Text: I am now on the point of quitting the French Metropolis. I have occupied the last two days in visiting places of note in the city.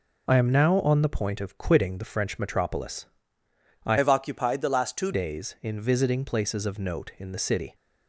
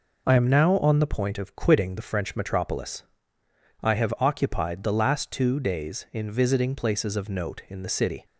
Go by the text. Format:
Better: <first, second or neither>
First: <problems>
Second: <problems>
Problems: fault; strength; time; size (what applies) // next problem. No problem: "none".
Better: second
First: changes voice from "have" to "two"; from 3.9 to 5.1 s; 1.2 s long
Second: none